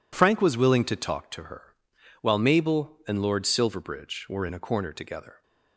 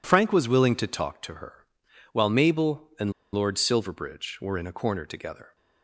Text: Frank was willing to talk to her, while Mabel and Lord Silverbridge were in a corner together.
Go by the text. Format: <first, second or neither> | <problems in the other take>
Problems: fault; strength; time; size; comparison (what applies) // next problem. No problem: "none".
first | pauses between "and" and "Lord"; slight; at 3.1 s; 0.22 s long